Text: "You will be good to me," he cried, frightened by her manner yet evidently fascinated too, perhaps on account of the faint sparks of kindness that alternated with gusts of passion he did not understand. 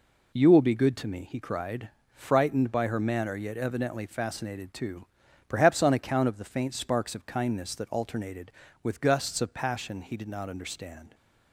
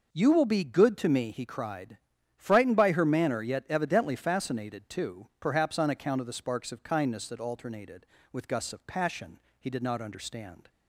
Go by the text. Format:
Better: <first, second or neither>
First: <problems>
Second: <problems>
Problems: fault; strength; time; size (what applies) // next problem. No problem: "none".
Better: first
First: none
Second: skips "faint"; at 6.3 s // pauses between "passion" and "he"; slight; at 9.3 s; 0.22 s long